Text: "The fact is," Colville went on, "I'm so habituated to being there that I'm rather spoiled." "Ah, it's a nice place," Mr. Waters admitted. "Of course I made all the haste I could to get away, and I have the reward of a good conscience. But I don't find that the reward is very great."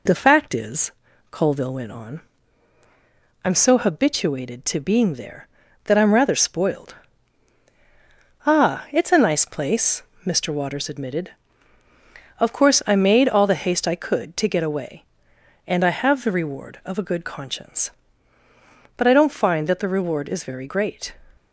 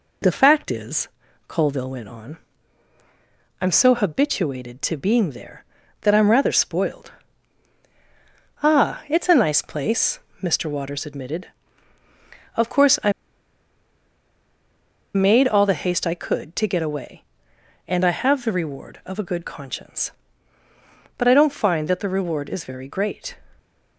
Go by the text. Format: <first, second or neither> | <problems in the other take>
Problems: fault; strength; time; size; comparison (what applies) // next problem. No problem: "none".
first | pauses between "I" and "made"; strong; at 13.1 s; 2.0 s long